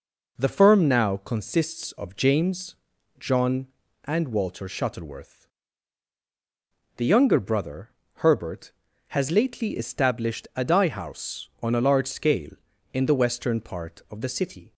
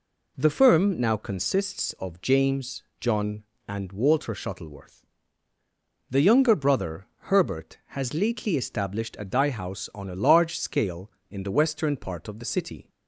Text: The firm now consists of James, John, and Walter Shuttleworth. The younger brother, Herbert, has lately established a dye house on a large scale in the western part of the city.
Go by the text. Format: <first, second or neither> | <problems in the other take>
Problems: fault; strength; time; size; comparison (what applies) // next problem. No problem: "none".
neither | none